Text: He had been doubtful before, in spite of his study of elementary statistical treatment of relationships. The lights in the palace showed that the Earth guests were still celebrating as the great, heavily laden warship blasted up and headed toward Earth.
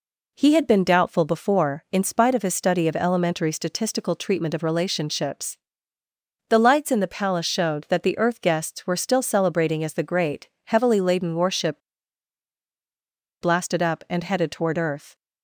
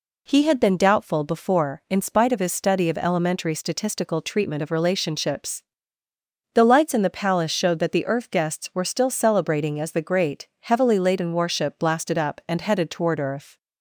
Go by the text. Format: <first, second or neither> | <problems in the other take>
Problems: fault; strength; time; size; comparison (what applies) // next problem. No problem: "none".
second | pauses between "warship" and "blasted"; strong; at 11.8 s; 1.6 s long